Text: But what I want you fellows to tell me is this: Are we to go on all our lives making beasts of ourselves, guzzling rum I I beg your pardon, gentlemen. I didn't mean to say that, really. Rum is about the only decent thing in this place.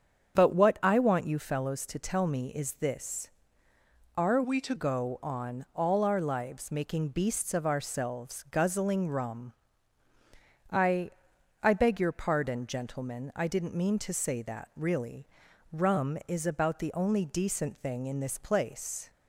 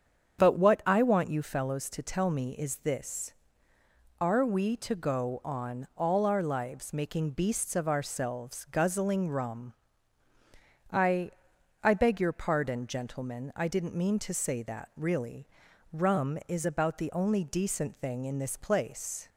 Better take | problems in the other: second | starts louder than the rest; strong; until 1.3 s; 7.5 dB; strong in the second // changes voice from "we" to "to"; from 4.4 to 4.7 s; 0.3 s long // pauses between "rum" and "I"; at 9.5 s; 1.2 s long; also in the second // pauses between "I" and "I"; noticeable; at 11.1 s; 0.50 s long; noticeable in the second

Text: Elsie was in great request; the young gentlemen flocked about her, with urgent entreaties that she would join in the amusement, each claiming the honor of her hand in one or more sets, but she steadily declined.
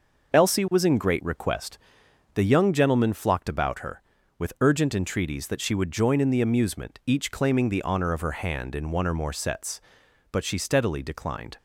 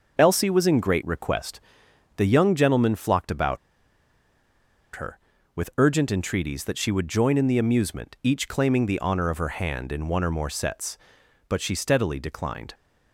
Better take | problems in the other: first | pauses between "about" and "her"; strong; at 3.5 s; 1.3 s long

